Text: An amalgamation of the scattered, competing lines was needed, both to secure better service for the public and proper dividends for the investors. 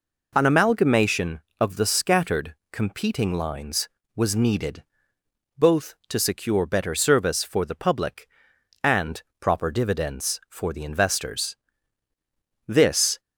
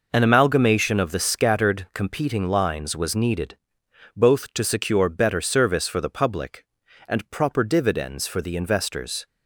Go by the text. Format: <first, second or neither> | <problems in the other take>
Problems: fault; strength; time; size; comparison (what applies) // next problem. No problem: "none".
second | pauses between "and" and "proper"; slight; at 9.2 s; 0.18 s long // goes on to say "This"; from 12.6 s on; 0.54 s long